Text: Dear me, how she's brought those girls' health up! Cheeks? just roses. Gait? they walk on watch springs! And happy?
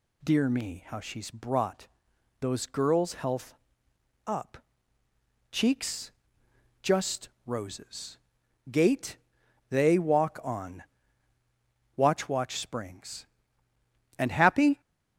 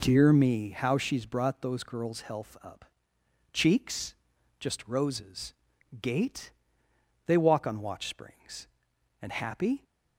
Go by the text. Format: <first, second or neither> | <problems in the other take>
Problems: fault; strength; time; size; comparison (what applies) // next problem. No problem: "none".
second | pauses between "brought" and "those"; noticeable; at 1.8 s; 0.54 s long // pauses between "health" and "up"; noticeable; at 3.5 s; 0.72 s long // pauses between "just" and "roses"; slight; at 7.2 s; 0.16 s long // pauses between "on" and "watch"; at 10.8 s; 1.1 s long // says "watch" twice; at 12.2 s